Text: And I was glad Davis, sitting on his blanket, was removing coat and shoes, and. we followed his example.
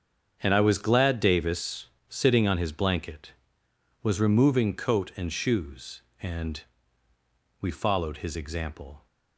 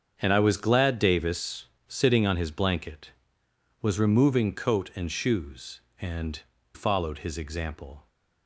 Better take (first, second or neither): first